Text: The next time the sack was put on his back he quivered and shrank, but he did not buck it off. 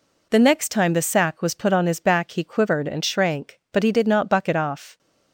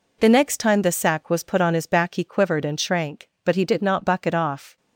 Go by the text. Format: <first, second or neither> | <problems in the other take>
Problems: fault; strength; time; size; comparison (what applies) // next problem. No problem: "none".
neither | none